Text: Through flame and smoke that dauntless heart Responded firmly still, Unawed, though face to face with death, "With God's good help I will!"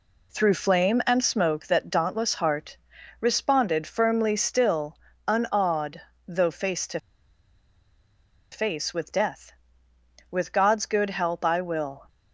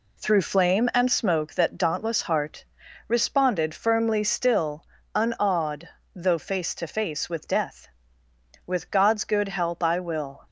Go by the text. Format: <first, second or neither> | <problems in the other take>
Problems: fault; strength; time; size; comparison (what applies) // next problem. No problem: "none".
second | pauses between "heart" and "Responded"; at 2.7 s; 0.42 s long; also in the second // pauses between "to" and "face"; strong; at 6.9 s; 1.5 s long